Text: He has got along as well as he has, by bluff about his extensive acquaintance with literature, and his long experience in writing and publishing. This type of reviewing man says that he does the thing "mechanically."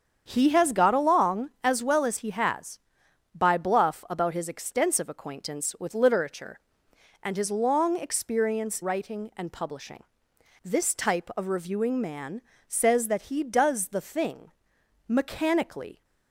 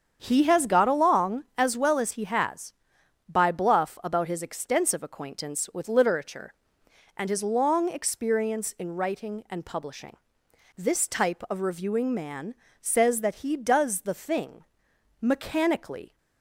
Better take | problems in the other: second | starts louder than the rest; strong; until 1.2 s; 7.5 dB; strong in the second // skips "in"; at 8.8 s // pauses between "man" and "says"; slight; at 12.3 s; 0.28 s long; slight in the second // pauses between "thing" and "mechanically"; noticeable; at 14.5 s; 0.56 s long; noticeable in the second

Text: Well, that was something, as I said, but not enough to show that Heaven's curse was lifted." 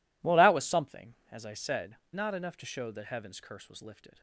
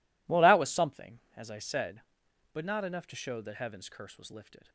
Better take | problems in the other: second | skips "but"; at 2.0 s

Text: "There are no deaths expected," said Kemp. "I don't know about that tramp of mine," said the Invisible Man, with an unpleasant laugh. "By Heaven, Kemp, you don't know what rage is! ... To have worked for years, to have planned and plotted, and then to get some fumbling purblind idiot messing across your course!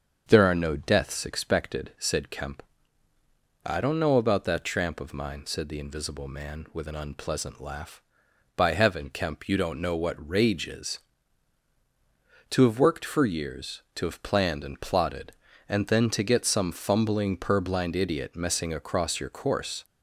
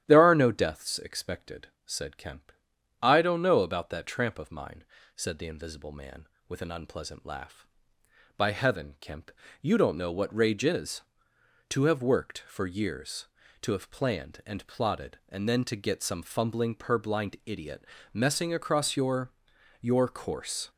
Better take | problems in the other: first | starts louder than the rest; strong; until 1.0 s; 11.5 dB; also in the first // pauses between "idiot" and "messing"; slight; at 17.8 s; 0.26 s long // says "your" twice; at 19.8 s

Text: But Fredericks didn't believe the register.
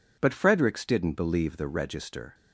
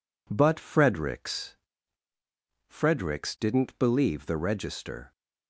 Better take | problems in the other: first | says "Fredericks" twice; at 2.6 s

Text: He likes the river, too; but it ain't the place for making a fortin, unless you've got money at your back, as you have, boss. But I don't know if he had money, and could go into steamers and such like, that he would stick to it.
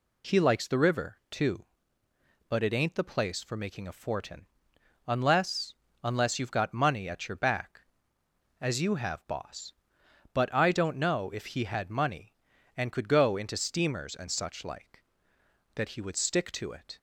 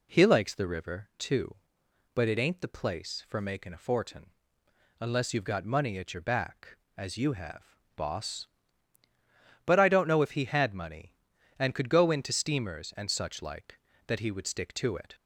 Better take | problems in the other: second | says "unless" twice; at 6.0 s

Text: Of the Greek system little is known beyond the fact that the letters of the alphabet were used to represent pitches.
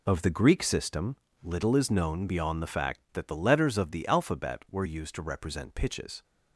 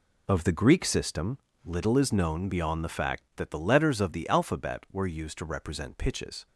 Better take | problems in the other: neither | pauses between "system" and "little"; slight; the same in both

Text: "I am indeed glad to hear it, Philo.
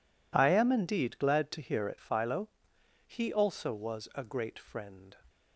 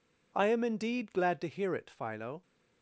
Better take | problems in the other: second | goes on to say "He also was a great friend"; strong; from 3.0 s on; 2.0 s long

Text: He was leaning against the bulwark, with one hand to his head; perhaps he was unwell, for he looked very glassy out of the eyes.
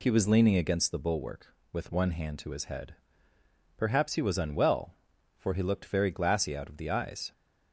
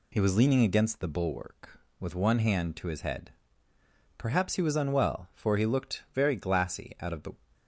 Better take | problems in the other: first | stops before "eyes"; at 7.5 s

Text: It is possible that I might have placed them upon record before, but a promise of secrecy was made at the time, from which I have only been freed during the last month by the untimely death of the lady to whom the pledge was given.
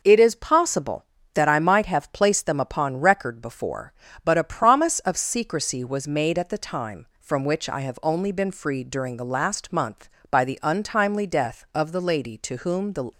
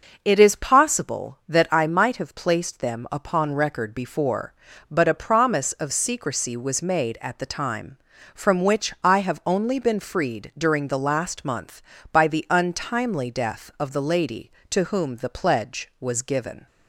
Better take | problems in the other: second | stops before "pledge was given"; at 13.1 s

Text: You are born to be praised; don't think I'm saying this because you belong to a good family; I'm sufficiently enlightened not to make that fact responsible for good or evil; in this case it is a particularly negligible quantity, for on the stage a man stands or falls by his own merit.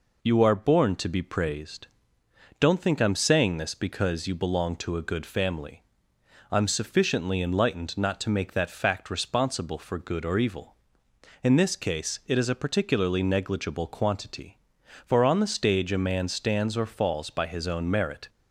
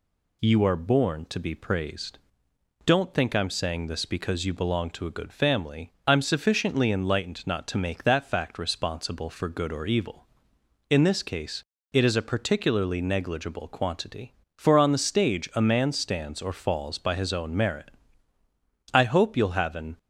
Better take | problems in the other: first | pauses between "case" and "it"; slight; at 11.6 s; 0.30 s long // goes on to say "I hope you'll have an"; noticeable; from 18.9 s on; 1.0 s long

